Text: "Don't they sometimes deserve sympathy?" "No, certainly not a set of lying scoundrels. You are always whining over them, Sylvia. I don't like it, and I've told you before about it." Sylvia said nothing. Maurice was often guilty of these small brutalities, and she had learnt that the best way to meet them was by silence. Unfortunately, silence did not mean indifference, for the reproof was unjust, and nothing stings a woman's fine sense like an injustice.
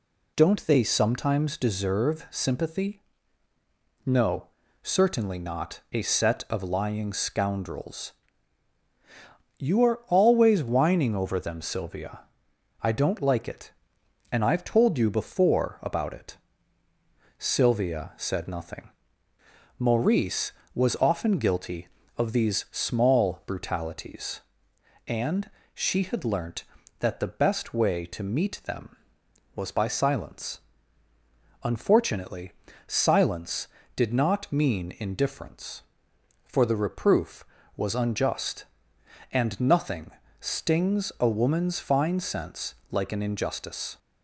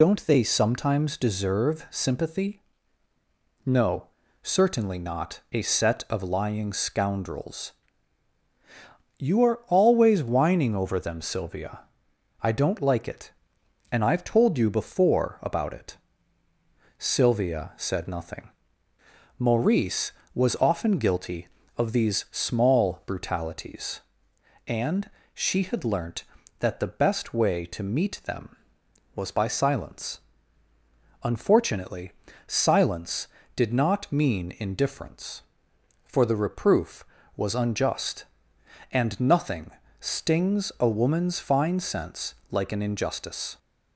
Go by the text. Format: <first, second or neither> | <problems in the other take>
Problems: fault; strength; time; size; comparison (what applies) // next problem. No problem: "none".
first | loses the start of "Don't"; at 0.0 s; 45 ms // pauses between "and" and "she"; slight; at 25.0 s; 0.24 s long; slight in the first // pauses between "nothing" and "stings"; slight; at 39.6 s; 0.30 s long; slight in the first // pauses between "sense" and "like"; slight; at 42.3 s; 0.16 s long; slight in the first